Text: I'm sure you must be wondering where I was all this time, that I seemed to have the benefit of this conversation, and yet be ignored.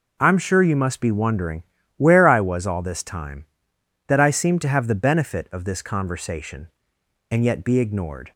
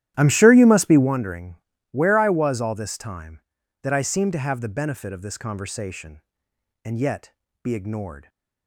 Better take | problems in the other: first | starts louder than the rest; strong; until 1.2 s; 12.5 dB // pauses between "wondering" and "where"; slight; at 1.5 s; 0.34 s long; slight in the first // pauses between "yet" and "be"; slight; at 7.3 s; 0.34 s long

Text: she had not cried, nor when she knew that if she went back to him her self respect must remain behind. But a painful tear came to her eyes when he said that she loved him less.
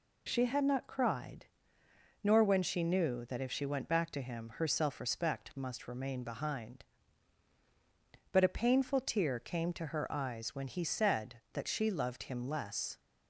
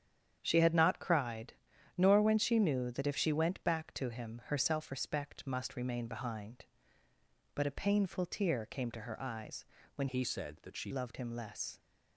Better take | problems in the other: first | starts louder than the rest; strong; until 1.4 s; 8.5 dB // pauses between "eyes" and "when"; slight; at 9.6 s; 0.32 s long // changes voice from "he" to "she"; from 10.0 to 10.9 s; 0.9 s long

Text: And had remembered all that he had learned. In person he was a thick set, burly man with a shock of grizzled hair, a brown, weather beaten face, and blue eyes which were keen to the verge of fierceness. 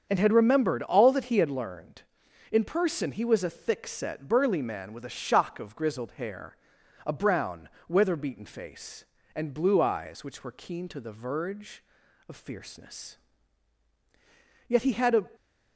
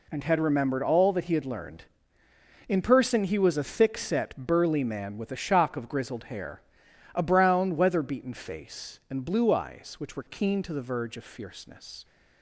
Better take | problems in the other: second | starts louder than the rest; strong; until 1.1 s; 7 dB // goes on to say "Yet he had a"; from 14.6 s on; 0.54 s long

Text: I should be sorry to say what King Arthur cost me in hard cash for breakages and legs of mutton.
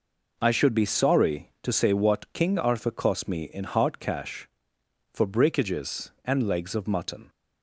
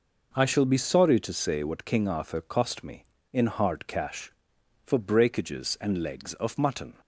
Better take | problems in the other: first | says "shall" for "should"; at 0.4 s

